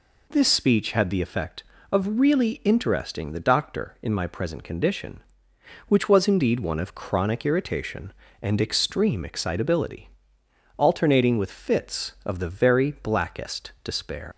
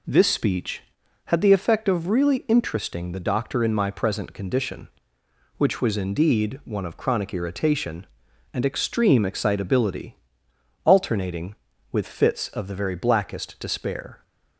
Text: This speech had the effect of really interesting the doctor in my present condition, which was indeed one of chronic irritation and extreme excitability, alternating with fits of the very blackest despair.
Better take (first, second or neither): second